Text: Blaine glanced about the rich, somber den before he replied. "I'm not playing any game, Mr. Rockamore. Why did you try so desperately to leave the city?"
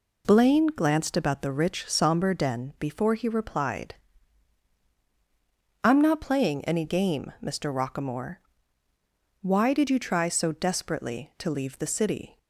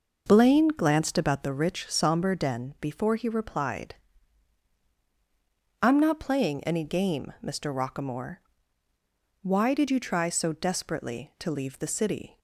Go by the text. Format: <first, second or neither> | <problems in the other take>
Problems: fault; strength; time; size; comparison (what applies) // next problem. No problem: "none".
first | starts louder than the rest; noticeable; until 1.5 s; 5.5 dB